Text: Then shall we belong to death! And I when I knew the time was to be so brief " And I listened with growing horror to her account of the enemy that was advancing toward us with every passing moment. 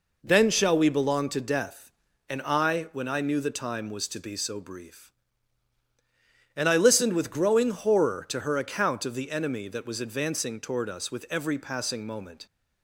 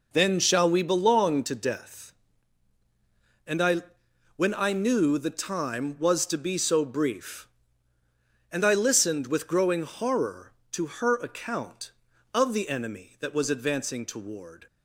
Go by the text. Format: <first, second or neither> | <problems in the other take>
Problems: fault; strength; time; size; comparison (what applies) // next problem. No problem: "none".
first | pauses between "I" and "when"; noticeable; at 3.8 s; 0.56 s long // stops before "us with every passing moment"; at 14.6 s